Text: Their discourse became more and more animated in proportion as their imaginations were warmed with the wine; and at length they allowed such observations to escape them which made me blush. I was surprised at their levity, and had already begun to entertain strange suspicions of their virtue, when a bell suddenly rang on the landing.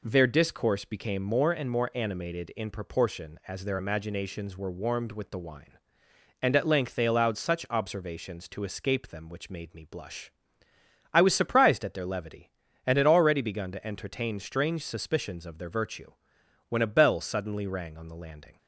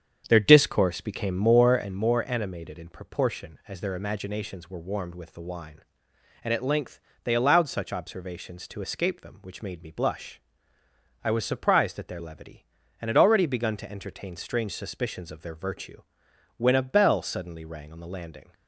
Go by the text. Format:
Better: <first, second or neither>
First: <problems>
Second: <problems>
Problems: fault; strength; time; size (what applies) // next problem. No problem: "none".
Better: first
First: none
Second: starts louder than the rest; strong; until 2.1 s; 8 dB // pauses between "length" and "they"; slight; at 6.9 s; 0.26 s long